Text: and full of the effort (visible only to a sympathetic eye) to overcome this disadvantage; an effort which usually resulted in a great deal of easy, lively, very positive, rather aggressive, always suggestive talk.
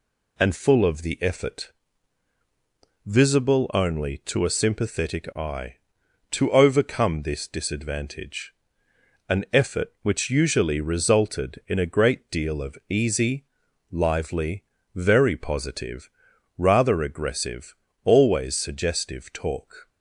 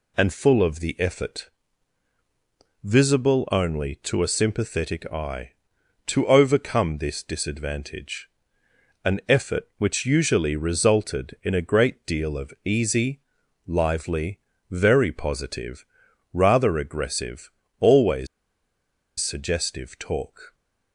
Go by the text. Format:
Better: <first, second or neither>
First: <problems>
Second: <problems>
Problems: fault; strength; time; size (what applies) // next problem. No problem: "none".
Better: first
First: none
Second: pauses between "always" and "suggestive"; noticeable; at 18.2 s; 0.93 s long